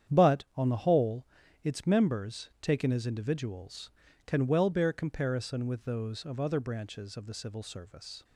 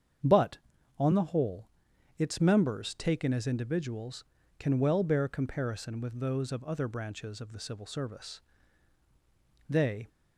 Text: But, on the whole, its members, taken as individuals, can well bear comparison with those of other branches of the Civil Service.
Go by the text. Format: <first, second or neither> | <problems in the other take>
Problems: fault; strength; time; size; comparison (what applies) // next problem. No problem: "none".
first | starts louder than the rest; strong; until 1.6 s; 7.5 dB; strong in the first // goes on to say "They"; slight; from 9.7 s on; 0.38 s long